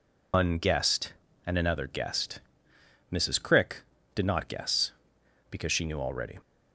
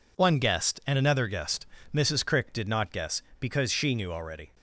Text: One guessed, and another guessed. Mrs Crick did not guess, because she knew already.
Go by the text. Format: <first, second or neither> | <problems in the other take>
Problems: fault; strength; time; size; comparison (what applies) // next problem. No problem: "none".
second | loses the start of "One"; at 0.3 s; 155 ms